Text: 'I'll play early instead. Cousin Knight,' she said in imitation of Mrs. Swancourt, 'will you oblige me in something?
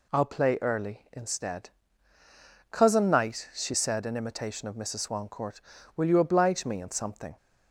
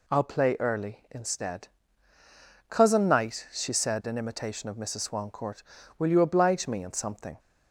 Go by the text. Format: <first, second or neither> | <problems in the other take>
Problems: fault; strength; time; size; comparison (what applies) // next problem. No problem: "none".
neither | none